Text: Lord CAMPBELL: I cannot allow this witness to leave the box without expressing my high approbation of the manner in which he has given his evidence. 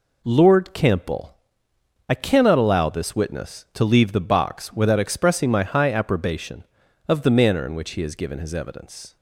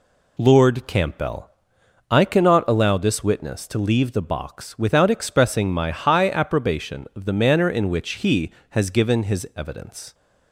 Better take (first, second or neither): neither